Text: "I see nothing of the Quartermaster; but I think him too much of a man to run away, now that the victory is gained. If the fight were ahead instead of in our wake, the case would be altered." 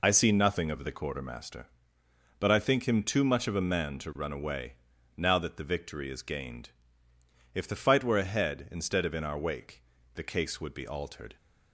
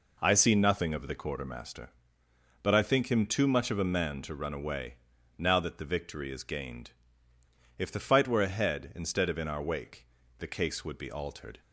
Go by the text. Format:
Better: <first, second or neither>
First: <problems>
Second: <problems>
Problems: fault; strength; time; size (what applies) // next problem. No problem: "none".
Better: second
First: loses the start of "I"; at 0.0 s; 65 ms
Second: none